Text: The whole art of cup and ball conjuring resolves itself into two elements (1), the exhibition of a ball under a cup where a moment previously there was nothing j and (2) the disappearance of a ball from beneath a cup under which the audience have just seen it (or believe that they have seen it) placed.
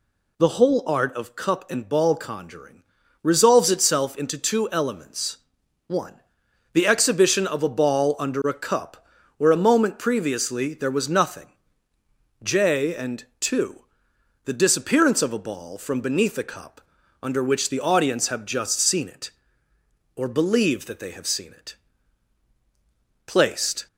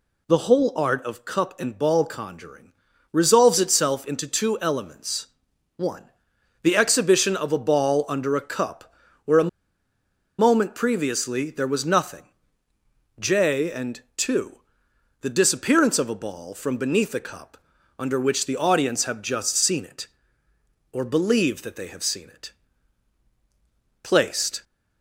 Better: first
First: pauses between "conjuring" and "resolves"; at 2.8 s; 0.40 s long // pauses between "cup" and "where"; slight; at 9.0 s; 0.36 s long // pauses between "nothing" and "j"; noticeable; at 11.5 s; 0.90 s long // pauses between "cup" and "under"; at 16.8 s; 0.42 s long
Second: pauses between "conjuring" and "resolves"; at 2.7 s; 0.40 s long // pauses between "cup" and "where"; slight; at 8.9 s; 0.36 s long // pauses between "a" and "moment"; noticeable; at 9.4 s; 0.91 s long // pauses between "nothing" and "j"; noticeable; at 12.2 s; 0.90 s long // pauses between "cup" and "under"; at 17.5 s; 0.42 s long

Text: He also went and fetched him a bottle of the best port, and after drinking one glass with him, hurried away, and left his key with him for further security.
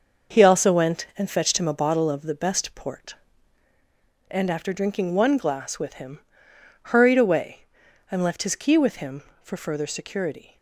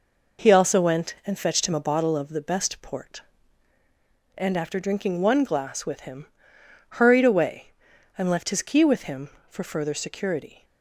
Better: second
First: gets quieter; strong; throughout; 8 dB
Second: none

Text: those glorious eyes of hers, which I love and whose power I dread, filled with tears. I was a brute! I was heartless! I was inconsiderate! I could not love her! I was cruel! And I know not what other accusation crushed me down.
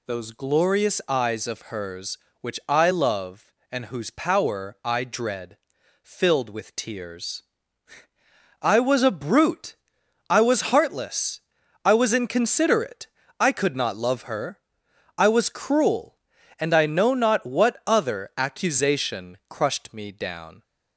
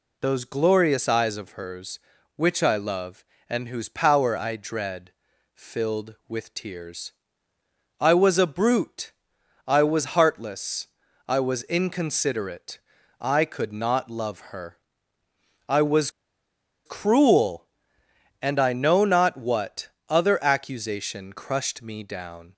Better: first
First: none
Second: pauses between "was" and "cruel"; noticeable; at 16.0 s; 0.76 s long // pauses between "what" and "other"; slight; at 19.8 s; 0.20 s long

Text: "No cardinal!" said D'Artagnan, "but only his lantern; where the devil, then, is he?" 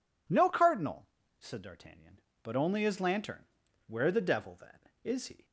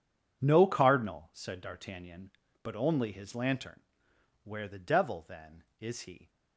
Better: neither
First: none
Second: none

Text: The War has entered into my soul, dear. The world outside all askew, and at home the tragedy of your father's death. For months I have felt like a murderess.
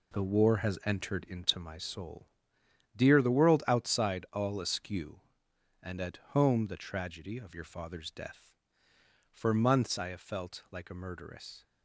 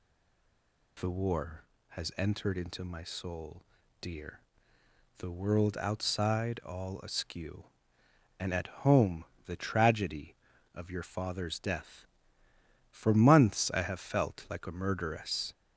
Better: first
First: none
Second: stays silent before the first word; slight; until 0.9 s; 0.9 s long // pauses between "home" and "the"; slight; at 9.2 s; 0.22 s long

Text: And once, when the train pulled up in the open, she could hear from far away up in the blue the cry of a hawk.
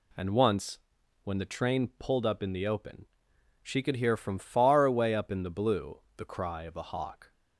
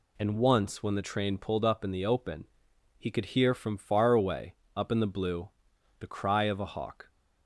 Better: first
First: pauses between "blue" and "the"; slight; at 5.9 s; 0.16 s long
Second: says "he" for "she"; at 2.9 s // pauses between "away" and "up"; slight; at 4.5 s; 0.20 s long // pauses between "blue" and "the"; noticeable; at 5.4 s; 0.50 s long

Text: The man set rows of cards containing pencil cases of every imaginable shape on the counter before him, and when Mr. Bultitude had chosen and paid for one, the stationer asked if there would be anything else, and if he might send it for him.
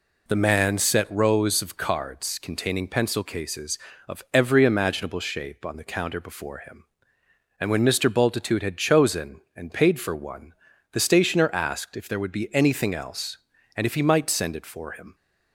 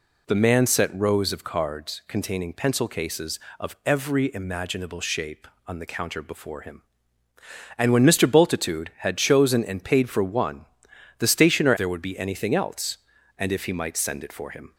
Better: first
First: none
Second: skips "asked if"; at 11.7 s

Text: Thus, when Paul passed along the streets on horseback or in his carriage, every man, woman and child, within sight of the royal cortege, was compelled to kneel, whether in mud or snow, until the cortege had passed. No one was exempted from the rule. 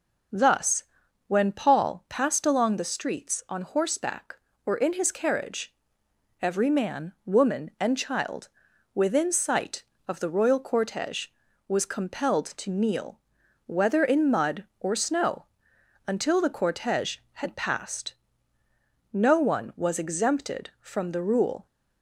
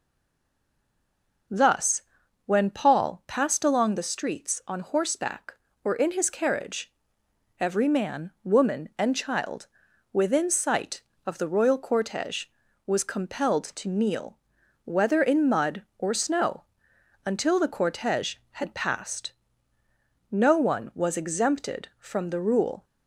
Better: first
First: none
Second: stays silent before the first word; noticeable; until 1.4 s; 1.4 s long

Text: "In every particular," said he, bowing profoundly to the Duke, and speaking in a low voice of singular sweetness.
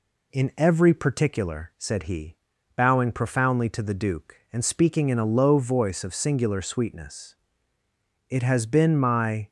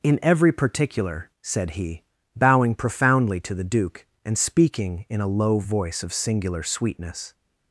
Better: second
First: goes on to say "It has been my"; noticeable; from 8.2 s on; 1.2 s long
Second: none

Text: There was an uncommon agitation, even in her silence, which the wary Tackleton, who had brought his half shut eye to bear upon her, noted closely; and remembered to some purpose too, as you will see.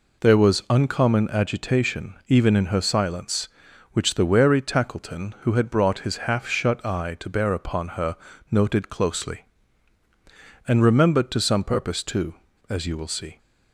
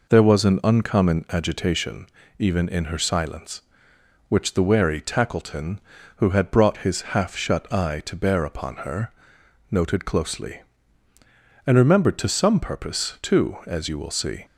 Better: second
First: skips "an"; at 0.6 s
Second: none

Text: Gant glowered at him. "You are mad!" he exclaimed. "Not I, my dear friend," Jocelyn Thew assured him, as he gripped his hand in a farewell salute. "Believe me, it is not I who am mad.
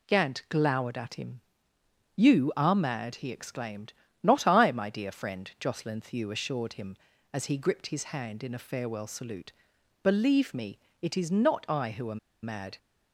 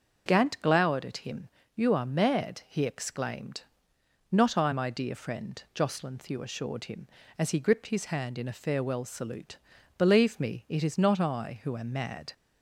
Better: second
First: pauses between "am" and "mad"; slight; at 12.1 s; 0.24 s long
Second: none

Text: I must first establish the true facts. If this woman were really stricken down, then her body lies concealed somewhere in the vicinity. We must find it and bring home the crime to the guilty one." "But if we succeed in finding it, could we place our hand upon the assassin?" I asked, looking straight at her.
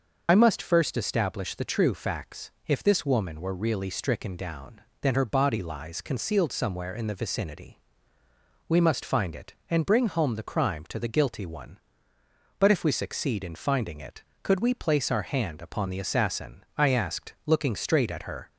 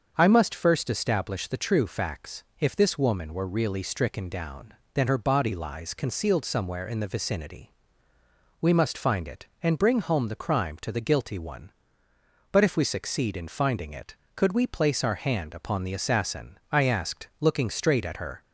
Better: second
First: loses the start of "I"; at 0.2 s; 55 ms // starts louder than the rest; noticeable; until 1.2 s; 6 dB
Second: starts louder than the rest; until 1.1 s; 6.5 dB

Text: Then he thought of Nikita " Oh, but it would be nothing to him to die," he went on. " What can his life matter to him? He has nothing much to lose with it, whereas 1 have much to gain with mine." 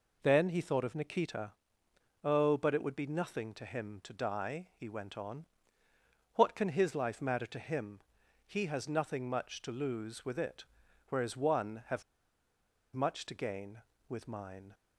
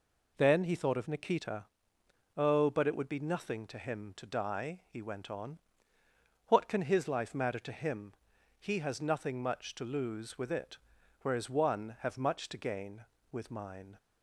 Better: second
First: pauses between "have" and "much"; noticeable; at 12.0 s; 0.90 s long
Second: none

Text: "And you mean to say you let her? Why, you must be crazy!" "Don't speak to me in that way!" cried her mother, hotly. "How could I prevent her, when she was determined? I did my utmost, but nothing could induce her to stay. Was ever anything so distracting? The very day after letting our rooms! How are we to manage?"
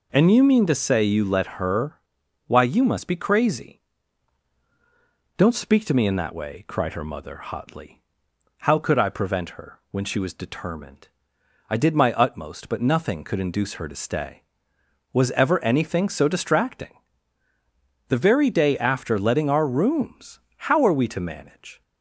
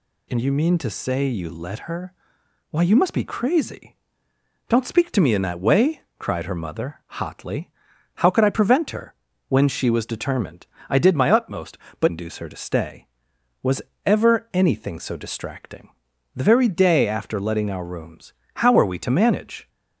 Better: first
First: none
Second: skips "nothing could"; at 12.0 s // pauses between "Was" and "ever"; slight; at 13.8 s; 0.24 s long

